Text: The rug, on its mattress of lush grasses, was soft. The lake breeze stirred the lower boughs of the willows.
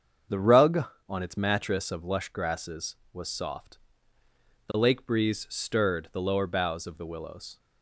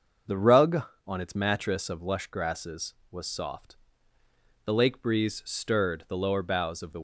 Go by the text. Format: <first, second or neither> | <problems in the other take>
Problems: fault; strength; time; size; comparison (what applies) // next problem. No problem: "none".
first | starts louder than the rest; until 1.5 s; 6.5 dB; strong in the first // stops before "willows"; at 6.9 s